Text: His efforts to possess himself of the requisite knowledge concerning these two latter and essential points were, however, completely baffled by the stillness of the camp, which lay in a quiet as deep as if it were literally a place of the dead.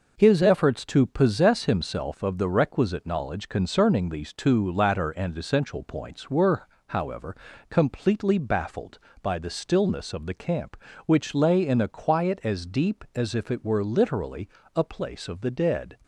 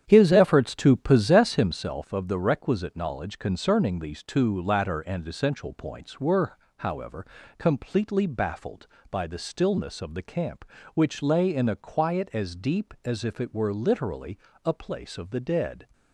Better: first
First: pauses between "literally" and "a"; slight; at 14.4 s; 0.28 s long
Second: starts louder than the rest; strong; until 1.8 s; 9 dB // pauses between "literally" and "a"; slight; at 14.3 s; 0.28 s long

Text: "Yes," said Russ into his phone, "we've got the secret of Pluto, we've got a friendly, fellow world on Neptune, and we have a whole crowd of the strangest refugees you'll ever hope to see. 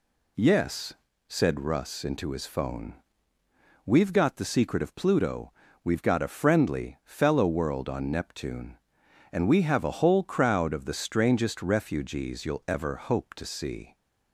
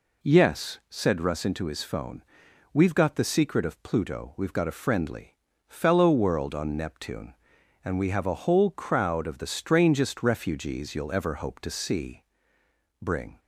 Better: first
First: none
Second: goes on to say "Bring"; slight; from 13.0 s on; 0.38 s long

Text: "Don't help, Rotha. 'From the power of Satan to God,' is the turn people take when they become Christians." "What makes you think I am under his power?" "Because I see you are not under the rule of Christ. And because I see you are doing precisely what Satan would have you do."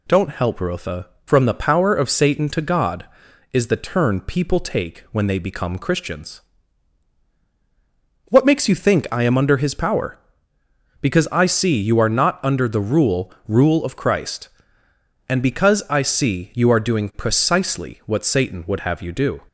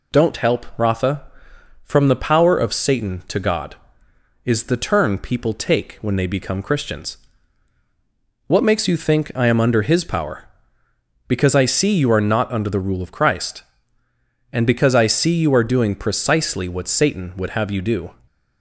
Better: second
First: says "rule" twice; at 13.4 s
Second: none

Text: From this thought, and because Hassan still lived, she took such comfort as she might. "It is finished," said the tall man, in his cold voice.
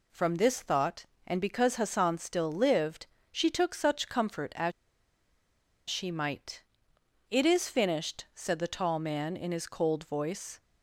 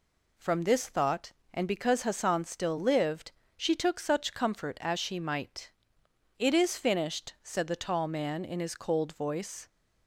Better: second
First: pauses between "as" and "she"; at 4.7 s; 1.1 s long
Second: none

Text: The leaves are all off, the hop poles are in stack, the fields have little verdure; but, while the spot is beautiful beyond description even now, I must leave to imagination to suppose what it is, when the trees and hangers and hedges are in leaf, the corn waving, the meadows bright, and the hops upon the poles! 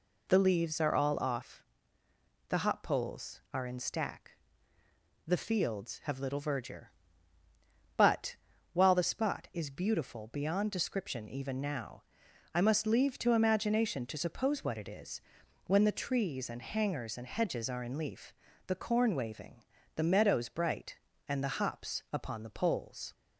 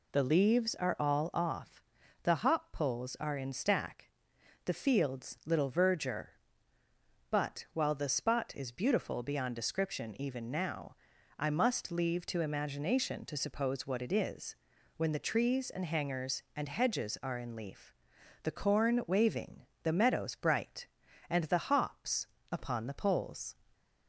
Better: first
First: none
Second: skips "have"; at 5.4 s // pauses between "hops" and "upon"; slight; at 22.2 s; 0.26 s long

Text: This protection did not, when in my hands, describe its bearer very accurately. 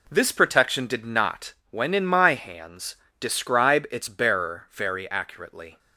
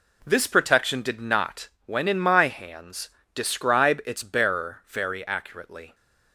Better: neither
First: none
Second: none

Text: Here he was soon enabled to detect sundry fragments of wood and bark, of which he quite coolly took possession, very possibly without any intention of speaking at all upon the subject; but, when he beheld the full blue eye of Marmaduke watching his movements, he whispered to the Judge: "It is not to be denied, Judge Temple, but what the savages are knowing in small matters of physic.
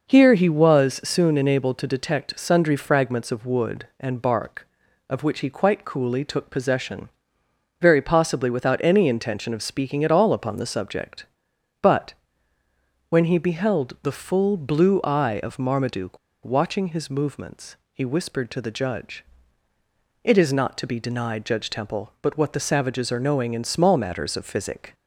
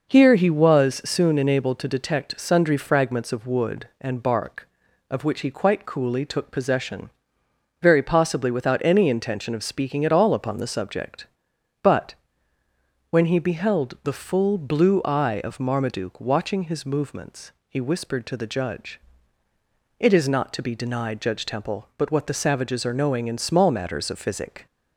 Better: second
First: pauses between "Marmaduke" and "watching"; slight; at 16.1 s; 0.28 s long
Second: none

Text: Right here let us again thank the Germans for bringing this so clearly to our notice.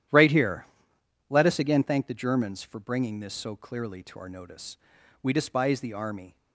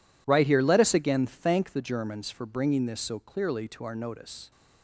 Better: second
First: starts louder than the rest; strong; until 1.7 s; 11 dB // pauses between "here" and "let"; noticeable; at 0.6 s; 0.64 s long // goes on to say "We despise the army"; noticeable; from 5.2 s on; 1.1 s long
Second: none

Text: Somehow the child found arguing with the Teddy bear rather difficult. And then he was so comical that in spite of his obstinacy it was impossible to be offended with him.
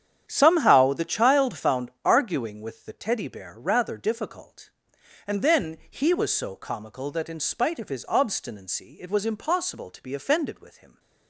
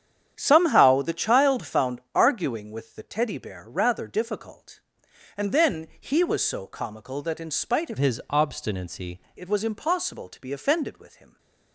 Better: first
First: starts louder than the rest; strong; until 1.2 s; 9 dB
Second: starts louder than the rest; strong; until 1.3 s; 9 dB // changes voice from "his" to "obstinacy"; from 7.9 to 9.1 s; 1.2 s long

